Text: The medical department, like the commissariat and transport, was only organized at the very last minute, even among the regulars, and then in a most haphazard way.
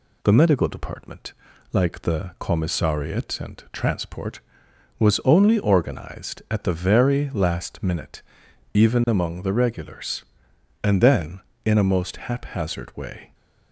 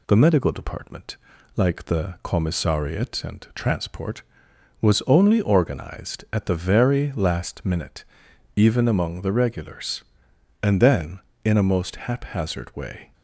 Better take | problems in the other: neither | none

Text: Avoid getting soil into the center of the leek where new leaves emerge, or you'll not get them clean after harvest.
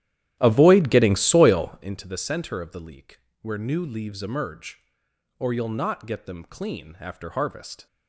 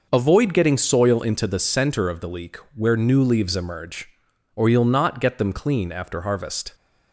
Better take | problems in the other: second | starts louder than the rest; strong; until 2.0 s; 12.5 dB // pauses between "leek" and "where"; slight; at 3.2 s; 0.22 s long; slight in the second

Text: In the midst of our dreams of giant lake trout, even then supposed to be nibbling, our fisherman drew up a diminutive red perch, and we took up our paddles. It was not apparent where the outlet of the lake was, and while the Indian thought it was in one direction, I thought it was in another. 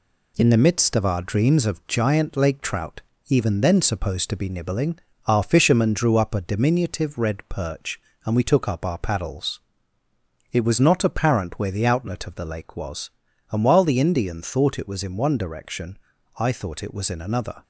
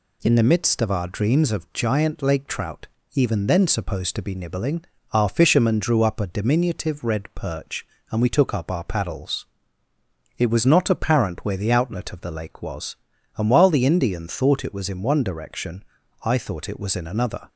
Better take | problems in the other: second | gets quieter; throughout; 3.5 dB

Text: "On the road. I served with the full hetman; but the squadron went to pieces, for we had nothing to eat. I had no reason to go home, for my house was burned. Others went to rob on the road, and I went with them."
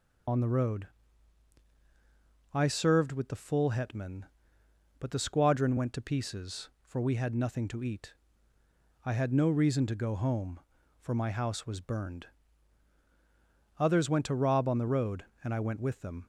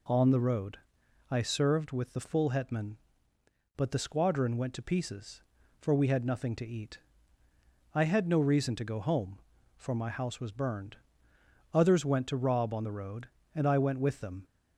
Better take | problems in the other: second | loses the start of "On"; at 0.2 s; 95 ms

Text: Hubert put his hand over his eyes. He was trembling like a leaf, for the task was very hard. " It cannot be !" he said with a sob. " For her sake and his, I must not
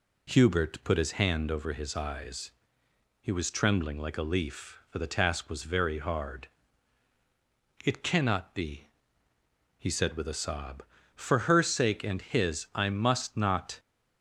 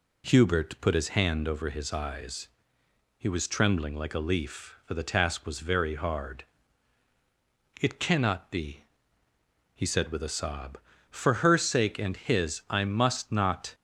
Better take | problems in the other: neither | none

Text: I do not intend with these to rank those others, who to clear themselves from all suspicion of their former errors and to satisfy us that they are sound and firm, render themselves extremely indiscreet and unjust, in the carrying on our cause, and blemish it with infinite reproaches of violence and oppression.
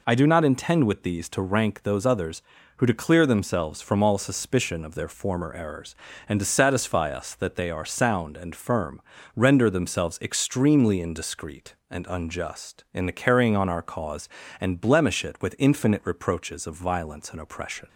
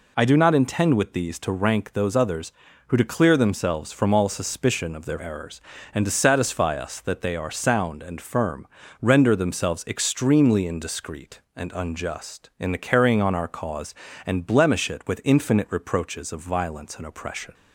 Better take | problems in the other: first | skips "former"; at 5.1 s

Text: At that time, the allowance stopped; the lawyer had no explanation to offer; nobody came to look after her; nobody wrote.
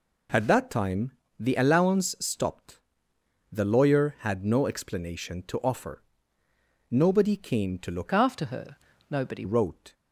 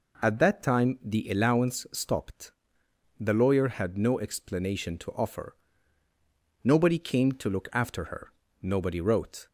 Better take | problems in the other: second | changes voice from "after" to "nobody"; from 8.1 to 9.4 s; 1.3 s long

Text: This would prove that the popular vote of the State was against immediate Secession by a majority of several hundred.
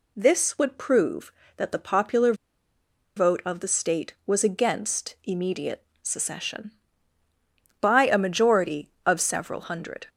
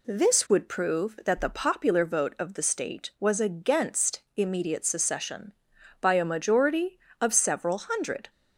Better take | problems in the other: second | pauses between "popular" and "vote"; noticeable; at 2.3 s; 0.82 s long // pauses between "immediate" and "Secession"; slight; at 5.8 s; 0.18 s long

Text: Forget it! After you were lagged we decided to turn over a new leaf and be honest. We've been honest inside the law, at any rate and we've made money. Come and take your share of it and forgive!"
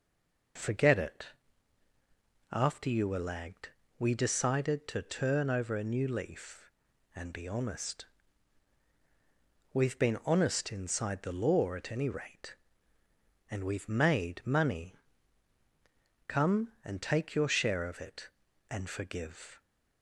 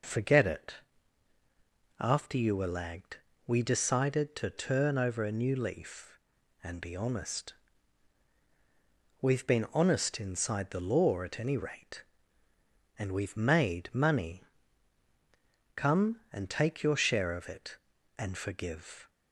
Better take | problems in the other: second | stays silent before the first word; slight; until 0.5 s; 0.5 s long // pauses between "lagged" and "we"; slight; at 3.6 s; 0.30 s long; slight in the second

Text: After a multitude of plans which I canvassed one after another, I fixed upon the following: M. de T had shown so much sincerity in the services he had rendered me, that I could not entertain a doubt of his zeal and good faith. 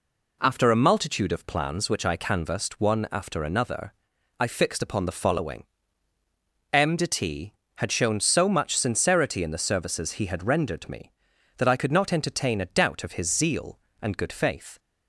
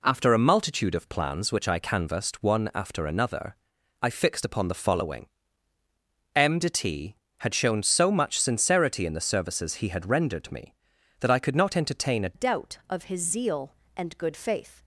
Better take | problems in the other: first | changes voice at "doubt"; from 12.3 s on; 2.5 s long

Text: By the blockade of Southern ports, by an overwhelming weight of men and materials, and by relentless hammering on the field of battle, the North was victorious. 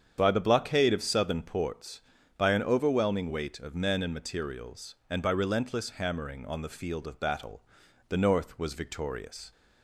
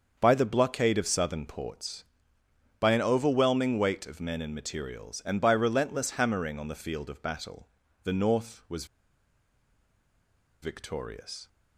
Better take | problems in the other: first | starts louder than the rest; until 1.2 s; 6.5 dB; strong in the first // pauses between "was" and "victorious"; strong; at 8.8 s; 1.7 s long

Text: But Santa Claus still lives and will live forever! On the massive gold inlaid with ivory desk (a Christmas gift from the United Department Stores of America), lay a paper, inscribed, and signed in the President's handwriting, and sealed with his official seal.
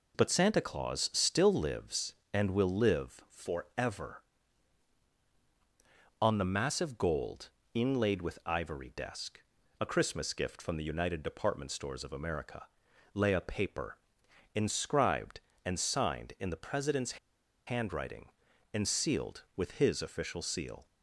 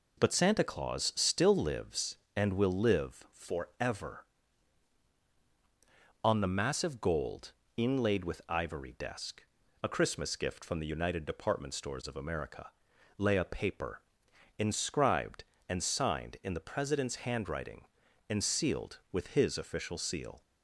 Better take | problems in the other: second | pauses between "gold" and "inlaid"; slight; at 7.4 s; 0.24 s long; slight in the second // pauses between "President's" and "handwriting"; noticeable; at 17.1 s; 0.48 s long

